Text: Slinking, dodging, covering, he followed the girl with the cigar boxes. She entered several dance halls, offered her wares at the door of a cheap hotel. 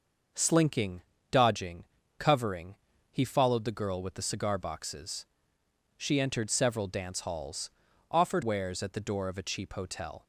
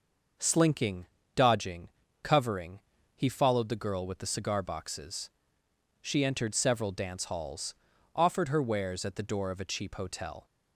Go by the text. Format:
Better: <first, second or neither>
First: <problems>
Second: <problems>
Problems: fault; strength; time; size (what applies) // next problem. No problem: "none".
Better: second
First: starts louder than the rest; noticeable; until 1.6 s; 6 dB // skips "her"; at 8.4 s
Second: none